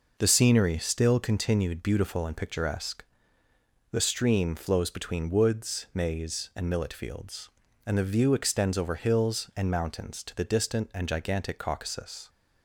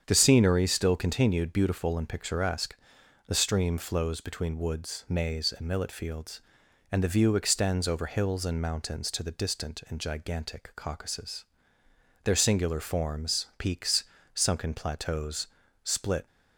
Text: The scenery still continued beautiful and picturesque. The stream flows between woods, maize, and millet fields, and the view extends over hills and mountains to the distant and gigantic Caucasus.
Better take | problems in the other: first | starts louder than the rest; strong; until 1.0 s; 8 dB // goes on to say "Their singular forms peaks sunken plateaus split"; strong; from 12.2 s on; 4.0 s long

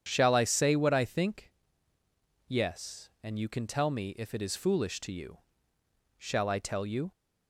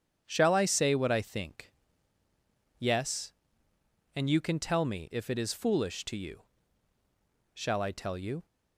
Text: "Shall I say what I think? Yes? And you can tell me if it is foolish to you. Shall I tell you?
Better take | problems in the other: neither | starts louder than the rest; strong; the same in both

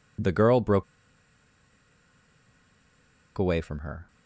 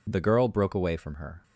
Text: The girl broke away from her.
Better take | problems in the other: second | pauses between "broke" and "away"; strong; at 0.8 s; 2.5 s long

